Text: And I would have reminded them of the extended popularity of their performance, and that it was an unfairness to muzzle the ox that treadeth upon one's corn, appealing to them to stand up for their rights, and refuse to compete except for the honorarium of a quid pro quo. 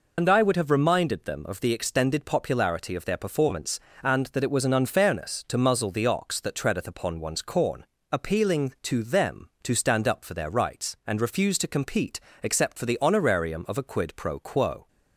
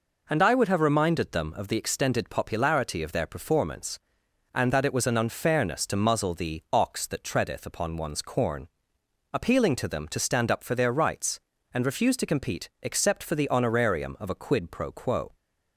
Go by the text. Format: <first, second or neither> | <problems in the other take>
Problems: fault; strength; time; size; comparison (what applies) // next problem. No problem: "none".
second | loses the start of "And"; at 0.1 s; 75 ms // pauses between "compete" and "except"; slight; at 12.2 s; 0.20 s long